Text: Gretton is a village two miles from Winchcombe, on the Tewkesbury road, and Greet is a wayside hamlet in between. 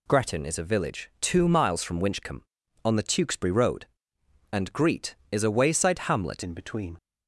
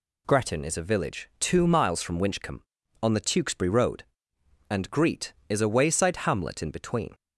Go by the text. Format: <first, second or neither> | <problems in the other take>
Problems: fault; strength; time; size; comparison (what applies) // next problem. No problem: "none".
second | changes voice at "in"; from 6.4 s on; 0.5 s long